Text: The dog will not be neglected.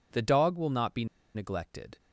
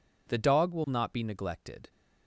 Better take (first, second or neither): second